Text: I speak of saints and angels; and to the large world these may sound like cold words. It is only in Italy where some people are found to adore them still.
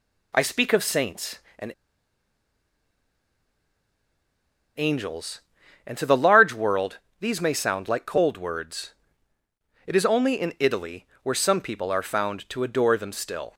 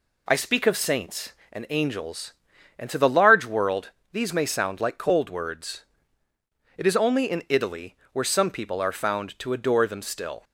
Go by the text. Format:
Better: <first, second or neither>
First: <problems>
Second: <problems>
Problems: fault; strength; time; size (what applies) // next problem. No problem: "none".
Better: second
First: pauses between "and" and "angels"; strong; at 1.7 s; 3.0 s long // pauses between "world" and "these"; slight; at 6.9 s; 0.22 s long // pauses between "Italy" and "where"; slight; at 11.0 s; 0.18 s long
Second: pauses between "world" and "these"; slight; at 3.9 s; 0.22 s long // pauses between "Italy" and "where"; slight; at 7.9 s; 0.18 s long